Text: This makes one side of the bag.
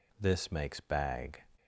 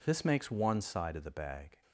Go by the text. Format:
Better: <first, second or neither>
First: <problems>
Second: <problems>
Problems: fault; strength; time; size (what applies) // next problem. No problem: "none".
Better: second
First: skips "one side of the"; at 0.8 s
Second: none